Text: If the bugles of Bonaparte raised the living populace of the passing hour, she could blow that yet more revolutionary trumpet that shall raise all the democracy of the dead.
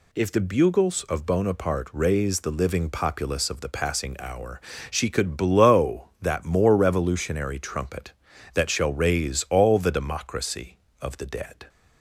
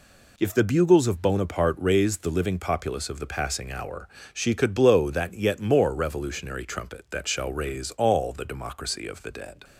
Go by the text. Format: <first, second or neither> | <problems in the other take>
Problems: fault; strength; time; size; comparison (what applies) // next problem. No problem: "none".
second | skips "yet"; at 6.4 s